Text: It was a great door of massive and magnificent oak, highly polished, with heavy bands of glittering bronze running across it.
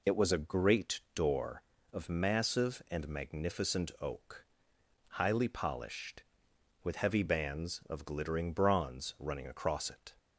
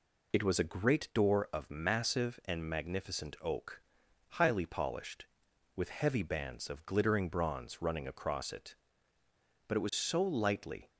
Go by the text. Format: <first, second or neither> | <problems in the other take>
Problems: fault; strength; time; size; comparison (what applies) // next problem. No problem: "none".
first | goes on to say "But it was so lightly"; noticeable; from 9.6 s on; 1.2 s long